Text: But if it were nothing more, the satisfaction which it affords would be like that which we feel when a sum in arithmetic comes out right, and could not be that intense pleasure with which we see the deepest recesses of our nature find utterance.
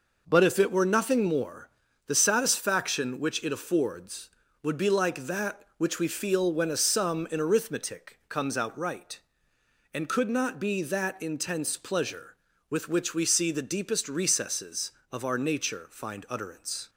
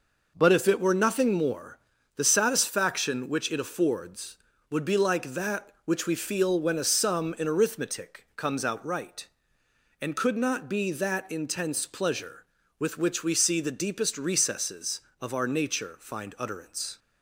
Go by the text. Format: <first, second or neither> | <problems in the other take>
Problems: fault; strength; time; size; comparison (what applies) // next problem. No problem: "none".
neither | none